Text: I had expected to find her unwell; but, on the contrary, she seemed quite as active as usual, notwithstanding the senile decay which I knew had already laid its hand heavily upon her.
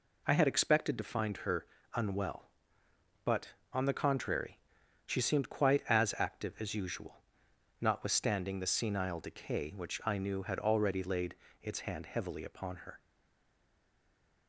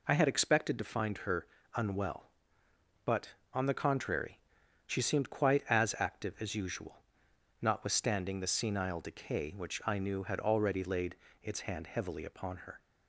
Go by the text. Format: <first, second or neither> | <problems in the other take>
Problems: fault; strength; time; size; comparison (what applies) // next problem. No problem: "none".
second | pauses between "her" and "unwell"; slight; at 1.6 s; 0.30 s long; slight in the second // pauses between "laid" and "its"; slight; at 11.3 s; 0.28 s long; slight in the second // stays silent after the last word; noticeable; from 13.0 s on; 1.4 s long